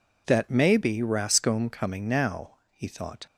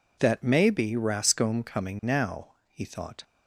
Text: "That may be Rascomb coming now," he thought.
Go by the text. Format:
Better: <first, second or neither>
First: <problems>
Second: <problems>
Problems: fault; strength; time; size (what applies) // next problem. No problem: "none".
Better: neither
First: none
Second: none